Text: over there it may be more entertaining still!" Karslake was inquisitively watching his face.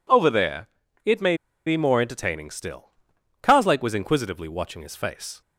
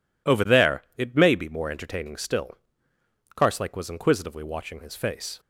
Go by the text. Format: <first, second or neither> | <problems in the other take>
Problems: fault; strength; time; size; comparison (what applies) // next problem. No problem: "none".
second | pauses between "there" and "it"; at 0.6 s; 0.38 s long // pauses between "may" and "be"; slight; at 1.3 s; 0.29 s long